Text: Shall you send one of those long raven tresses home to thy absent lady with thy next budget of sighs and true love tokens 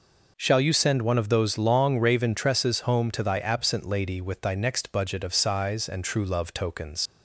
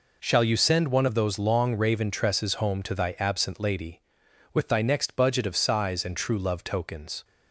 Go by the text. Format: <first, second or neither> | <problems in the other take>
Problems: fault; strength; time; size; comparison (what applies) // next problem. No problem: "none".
second | leaves "tokens" unfinished; at 7.0 s; 85 ms